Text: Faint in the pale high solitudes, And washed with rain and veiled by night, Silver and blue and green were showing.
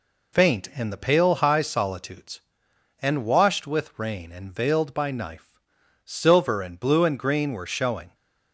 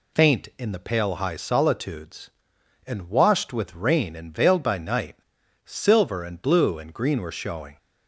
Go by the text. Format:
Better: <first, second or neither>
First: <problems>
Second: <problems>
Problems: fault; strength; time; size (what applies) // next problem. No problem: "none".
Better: second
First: says "knife" for "night"; at 5.1 s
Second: none